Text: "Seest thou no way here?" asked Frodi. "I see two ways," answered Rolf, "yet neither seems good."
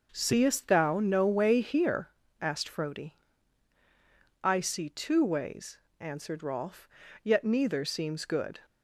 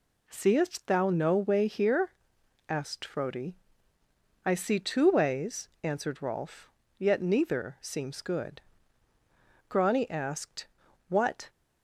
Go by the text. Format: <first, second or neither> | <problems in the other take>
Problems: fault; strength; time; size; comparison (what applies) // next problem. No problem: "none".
first | goes on to say "Grani asked What"; strong; from 9.6 s on; 1.8 s long